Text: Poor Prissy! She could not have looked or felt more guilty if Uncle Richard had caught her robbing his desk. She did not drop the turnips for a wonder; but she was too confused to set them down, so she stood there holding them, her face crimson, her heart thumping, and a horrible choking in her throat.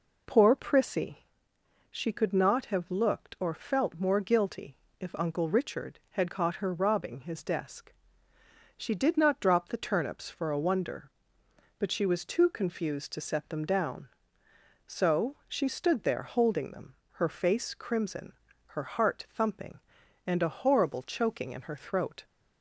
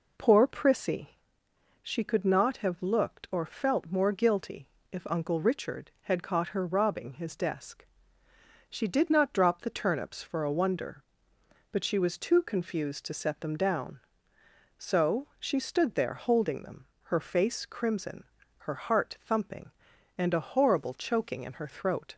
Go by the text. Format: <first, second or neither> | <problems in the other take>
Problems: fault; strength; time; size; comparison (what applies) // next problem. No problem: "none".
neither | pauses between "guilty" and "if"; slight; the same in both